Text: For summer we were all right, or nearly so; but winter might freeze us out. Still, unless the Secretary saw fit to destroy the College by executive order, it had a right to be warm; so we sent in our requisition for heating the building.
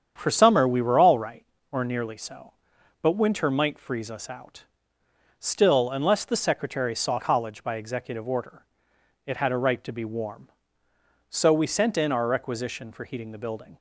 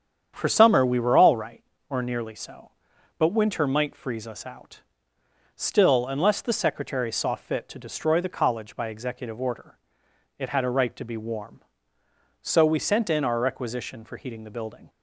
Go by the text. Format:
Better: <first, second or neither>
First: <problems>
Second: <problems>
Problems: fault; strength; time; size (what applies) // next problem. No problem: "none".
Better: second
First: starts louder than the rest; strong; until 1.1 s; 8 dB // skips "fit to destroy the"; at 7.1 s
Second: starts louder than the rest; strong; until 1.3 s; 8.5 dB